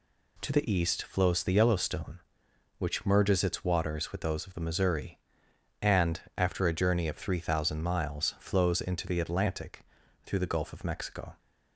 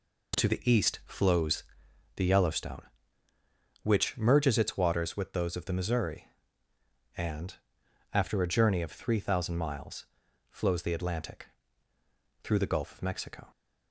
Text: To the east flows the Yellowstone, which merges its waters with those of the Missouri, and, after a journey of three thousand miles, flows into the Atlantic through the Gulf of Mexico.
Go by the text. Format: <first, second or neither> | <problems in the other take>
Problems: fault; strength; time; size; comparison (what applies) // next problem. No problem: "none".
first | pauses between "flows" and "the"; noticeable; at 1.6 s; 0.54 s long // skips "into"; at 10.8 s // pauses between "Atlantic" and "through"; noticeable; at 11.4 s; 0.96 s long; also in the first